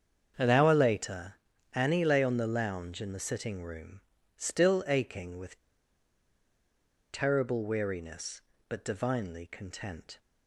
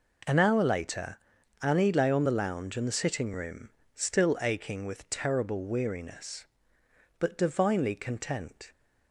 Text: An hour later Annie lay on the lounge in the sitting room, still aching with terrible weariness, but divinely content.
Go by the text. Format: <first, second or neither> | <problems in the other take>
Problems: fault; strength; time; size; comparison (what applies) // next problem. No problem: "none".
second | starts louder than the rest; strong; until 1.7 s; 7 dB // pauses between "later" and "Annie"; at 1.3 s; 0.42 s long; also in the second // pauses between "with" and "terrible"; strong; at 5.5 s; 1.5 s long